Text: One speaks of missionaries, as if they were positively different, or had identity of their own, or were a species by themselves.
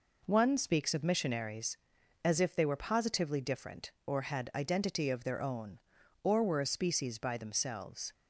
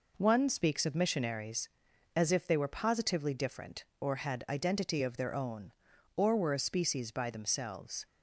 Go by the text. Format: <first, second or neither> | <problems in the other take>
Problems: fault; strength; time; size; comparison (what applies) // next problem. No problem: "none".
neither | none